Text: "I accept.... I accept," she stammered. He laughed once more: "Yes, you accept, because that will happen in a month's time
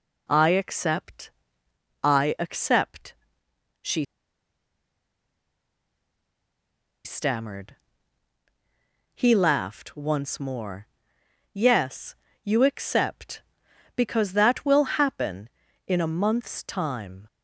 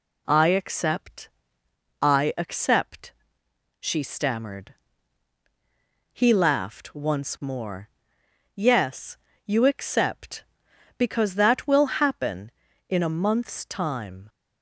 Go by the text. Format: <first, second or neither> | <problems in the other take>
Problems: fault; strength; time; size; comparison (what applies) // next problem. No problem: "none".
second | pauses between "she" and "stammered"; strong; at 4.0 s; 3.0 s long